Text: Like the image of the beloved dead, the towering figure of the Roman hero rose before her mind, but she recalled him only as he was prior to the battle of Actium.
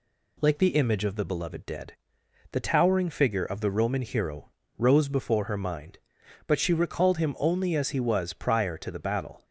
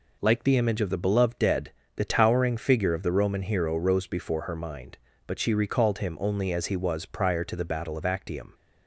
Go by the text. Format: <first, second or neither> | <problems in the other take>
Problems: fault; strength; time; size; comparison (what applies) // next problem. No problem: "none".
second | pauses between "hero" and "rose"; slight; at 4.5 s; 0.26 s long // stops before "of Actium"; at 9.4 s